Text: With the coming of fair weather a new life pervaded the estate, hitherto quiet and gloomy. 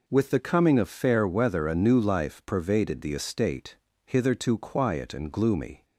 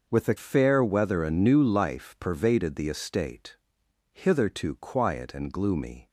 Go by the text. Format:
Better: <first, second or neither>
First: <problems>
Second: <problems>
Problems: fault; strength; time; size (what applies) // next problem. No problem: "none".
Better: first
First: none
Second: skips "coming of"; at 0.3 s